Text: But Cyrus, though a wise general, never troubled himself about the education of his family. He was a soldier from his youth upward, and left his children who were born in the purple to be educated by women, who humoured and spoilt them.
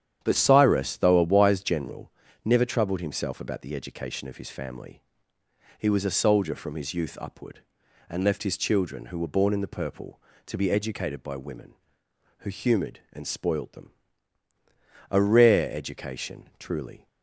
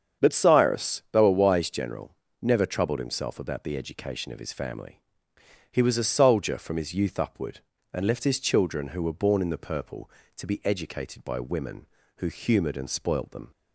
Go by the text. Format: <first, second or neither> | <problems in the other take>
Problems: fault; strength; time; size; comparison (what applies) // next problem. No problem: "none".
second | starts louder than the rest; strong; until 1.2 s; 9.5 dB; strong in the second // goes on to say "A rare education truly"; strong; from 15.0 s on; 1.9 s long